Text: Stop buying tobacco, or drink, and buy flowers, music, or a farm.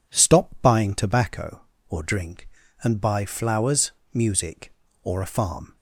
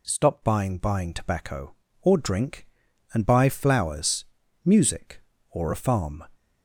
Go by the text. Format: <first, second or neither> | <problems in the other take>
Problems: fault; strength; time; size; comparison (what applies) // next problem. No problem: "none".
first | says "buying" twice; at 0.7 s